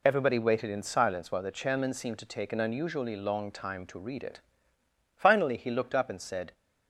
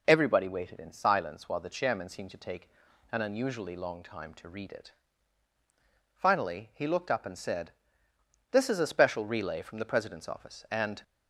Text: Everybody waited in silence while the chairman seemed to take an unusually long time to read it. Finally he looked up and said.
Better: first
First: none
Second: pauses between "take" and "an"; at 2.6 s; 0.44 s long // goes on to say "This is a special relay from the President's office and"; strong; from 8.5 s on; 2.5 s long

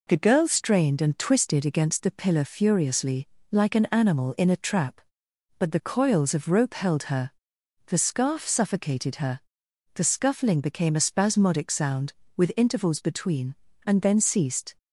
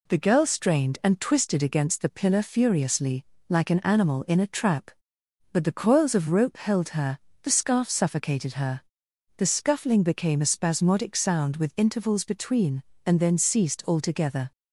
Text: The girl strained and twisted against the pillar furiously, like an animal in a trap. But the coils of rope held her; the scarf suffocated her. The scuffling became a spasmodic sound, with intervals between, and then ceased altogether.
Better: second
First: stops before "altogether"; at 14.7 s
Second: none

